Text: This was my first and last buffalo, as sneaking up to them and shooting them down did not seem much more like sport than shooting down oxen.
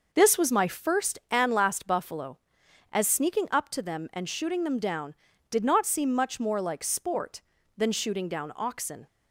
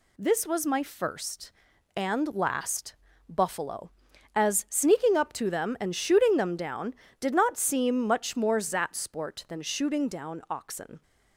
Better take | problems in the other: first | pauses between "last" and "buffalo"; slight; at 2.9 s; 0.34 s long // says "zat" for "like"; at 8.5 s

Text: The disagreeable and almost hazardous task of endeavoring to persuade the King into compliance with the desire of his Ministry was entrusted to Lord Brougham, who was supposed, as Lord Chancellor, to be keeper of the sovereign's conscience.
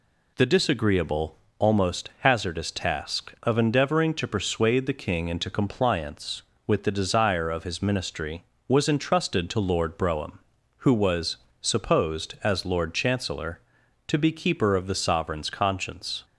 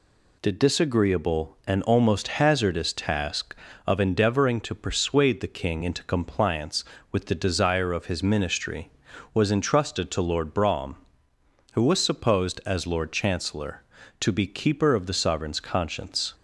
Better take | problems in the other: second | skips "and"; at 1.4 s // pauses between "was" and "supposed"; slight; at 11.3 s; 0.26 s long

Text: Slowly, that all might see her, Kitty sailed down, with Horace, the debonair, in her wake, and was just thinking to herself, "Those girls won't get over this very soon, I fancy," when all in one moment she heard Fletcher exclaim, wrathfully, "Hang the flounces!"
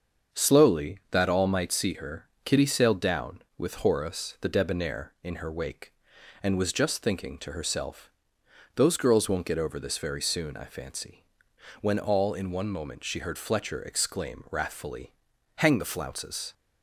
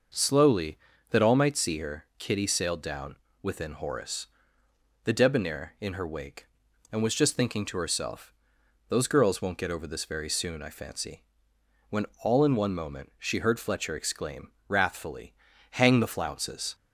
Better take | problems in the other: first | starts louder than the rest; noticeable; until 1.4 s; 6 dB; also in the first // says "within" for "with"; at 3.4 s // pauses between "when" and "all"; slight; at 12.0 s; 0.18 s long

